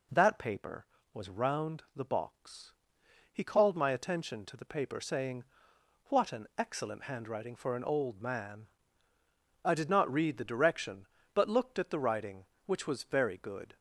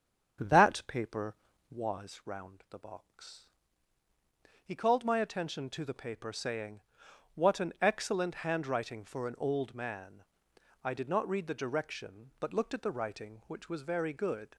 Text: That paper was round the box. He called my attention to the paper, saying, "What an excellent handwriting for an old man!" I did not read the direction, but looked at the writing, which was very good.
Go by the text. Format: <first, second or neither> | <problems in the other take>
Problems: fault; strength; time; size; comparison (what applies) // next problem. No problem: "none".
first | starts louder than the rest; strong; until 1.8 s; 7.5 dB